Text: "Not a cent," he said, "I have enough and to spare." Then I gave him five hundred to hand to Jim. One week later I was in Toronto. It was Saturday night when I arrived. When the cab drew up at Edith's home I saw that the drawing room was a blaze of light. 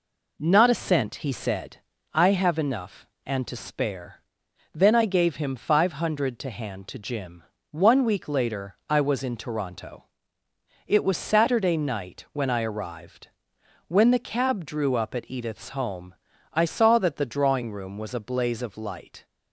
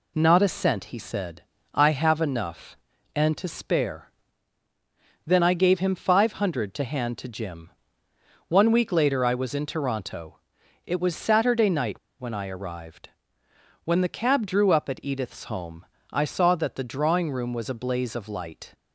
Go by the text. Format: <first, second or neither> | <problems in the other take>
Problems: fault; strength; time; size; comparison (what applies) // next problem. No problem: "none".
first | pauses between "night" and "when"; slight; at 11.9 s; 0.20 s long // pauses between "home" and "I"; slight; at 15.8 s; 0.26 s long; slight in the first